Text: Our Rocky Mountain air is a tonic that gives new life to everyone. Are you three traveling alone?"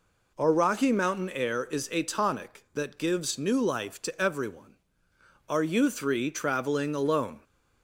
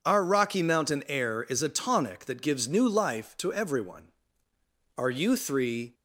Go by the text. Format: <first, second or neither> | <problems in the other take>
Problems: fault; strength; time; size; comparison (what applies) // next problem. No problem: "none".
first | stops before "traveling alone"; at 5.9 s